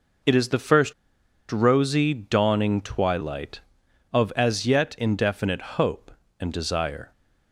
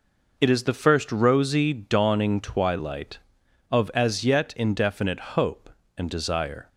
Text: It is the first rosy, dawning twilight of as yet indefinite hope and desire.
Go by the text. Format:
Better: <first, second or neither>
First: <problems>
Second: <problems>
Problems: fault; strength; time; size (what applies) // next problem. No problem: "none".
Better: second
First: pauses between "first" and "rosy"; noticeable; at 0.9 s; 0.57 s long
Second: none